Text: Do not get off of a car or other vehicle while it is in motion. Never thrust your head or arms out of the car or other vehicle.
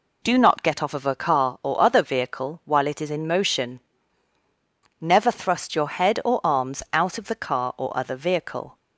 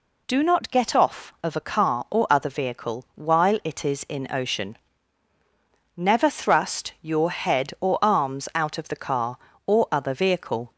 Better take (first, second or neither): first